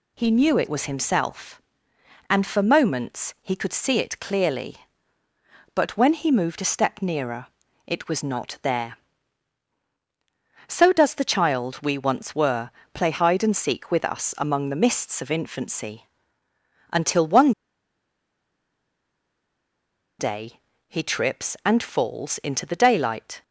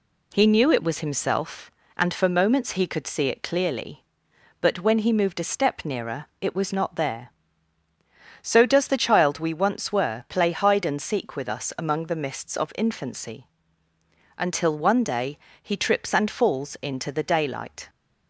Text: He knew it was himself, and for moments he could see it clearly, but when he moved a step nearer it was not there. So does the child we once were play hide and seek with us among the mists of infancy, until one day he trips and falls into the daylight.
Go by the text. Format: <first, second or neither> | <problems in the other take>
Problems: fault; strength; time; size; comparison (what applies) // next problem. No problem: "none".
second | pauses between "nearer" and "it"; at 7.4 s; 0.38 s long; slight in the second // pauses between "were" and "play"; slight; at 12.7 s; 0.22 s long // pauses between "one" and "day"; strong; at 17.5 s; 2.6 s long // pauses between "day" and "he"; slight; at 20.5 s; 0.30 s long; slight in the second